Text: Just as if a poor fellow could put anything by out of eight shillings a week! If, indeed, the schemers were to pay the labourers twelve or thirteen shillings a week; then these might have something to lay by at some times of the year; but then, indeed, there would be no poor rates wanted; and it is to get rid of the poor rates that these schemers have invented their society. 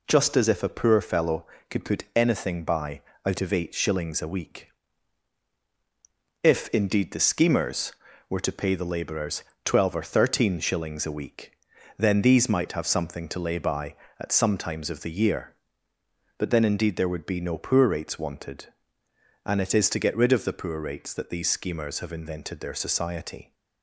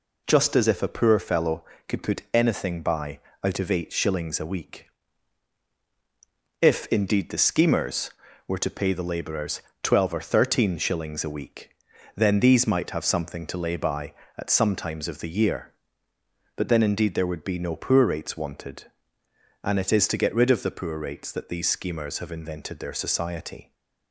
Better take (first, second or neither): neither